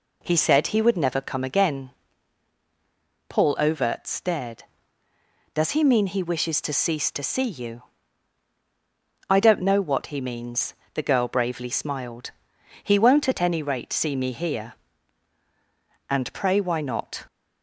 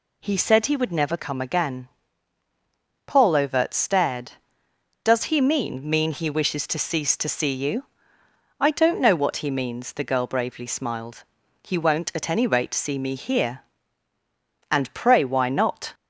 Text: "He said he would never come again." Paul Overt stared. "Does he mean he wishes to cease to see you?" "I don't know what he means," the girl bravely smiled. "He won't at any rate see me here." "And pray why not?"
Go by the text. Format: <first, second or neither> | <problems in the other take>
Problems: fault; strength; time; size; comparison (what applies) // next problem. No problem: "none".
first | says "mean" twice; at 5.8 s